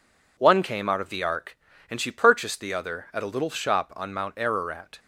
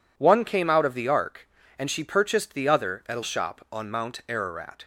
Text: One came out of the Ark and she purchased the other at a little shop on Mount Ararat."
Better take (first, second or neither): first